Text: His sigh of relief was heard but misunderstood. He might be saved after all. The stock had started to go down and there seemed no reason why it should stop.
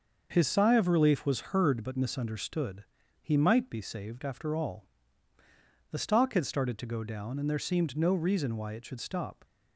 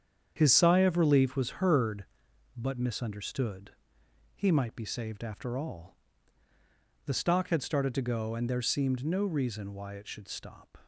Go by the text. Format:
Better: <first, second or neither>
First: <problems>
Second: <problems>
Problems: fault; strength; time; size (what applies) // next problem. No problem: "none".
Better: first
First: starts louder than the rest; until 1.3 s; 6 dB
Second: starts louder than the rest; strong; until 1.3 s; 8 dB // skips "down"; at 8.3 s